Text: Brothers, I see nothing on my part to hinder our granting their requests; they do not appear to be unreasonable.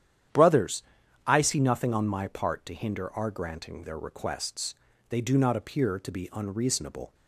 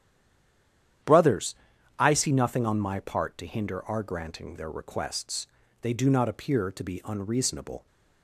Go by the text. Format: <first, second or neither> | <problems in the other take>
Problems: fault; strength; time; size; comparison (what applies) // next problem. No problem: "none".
first | stays silent before the first word; until 1.0 s; 1.0 s long // starts louder than the rest; strong; until 2.4 s; 10.5 dB; strong in the first